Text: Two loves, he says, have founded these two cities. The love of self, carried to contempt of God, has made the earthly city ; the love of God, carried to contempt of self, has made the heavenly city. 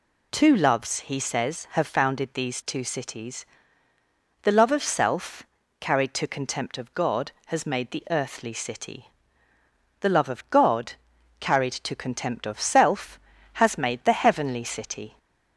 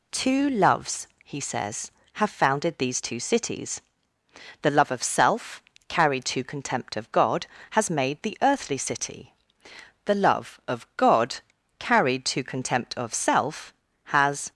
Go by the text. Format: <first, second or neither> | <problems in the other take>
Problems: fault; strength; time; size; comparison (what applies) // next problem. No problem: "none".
first | stops before "made the heavenly city"; at 14.5 s